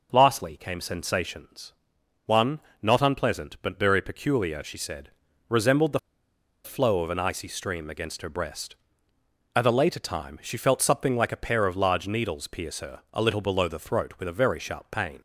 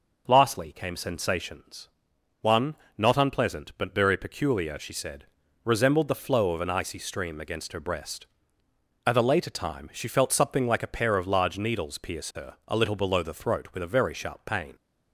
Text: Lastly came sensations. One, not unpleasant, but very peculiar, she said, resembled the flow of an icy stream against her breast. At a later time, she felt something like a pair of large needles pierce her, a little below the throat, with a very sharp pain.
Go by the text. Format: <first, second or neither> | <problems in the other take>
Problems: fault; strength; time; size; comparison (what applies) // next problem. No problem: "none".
second | pauses between "the" and "flow"; noticeable; at 5.9 s; 0.64 s long